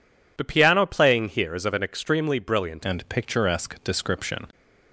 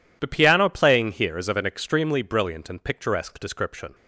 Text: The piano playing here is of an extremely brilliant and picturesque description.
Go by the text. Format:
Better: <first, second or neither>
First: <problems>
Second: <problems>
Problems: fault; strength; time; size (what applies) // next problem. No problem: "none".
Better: second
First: changes voice at "and"; from 2.8 s on; 1.6 s long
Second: none